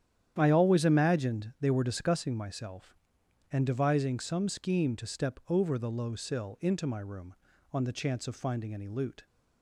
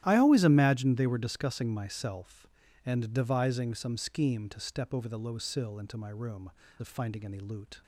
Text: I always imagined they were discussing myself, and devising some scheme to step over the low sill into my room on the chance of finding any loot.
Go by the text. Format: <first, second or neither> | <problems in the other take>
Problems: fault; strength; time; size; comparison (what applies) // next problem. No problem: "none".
first | starts louder than the rest; strong; until 1.0 s; 13 dB; strong in the first // skips "on the chance"; at 6.6 s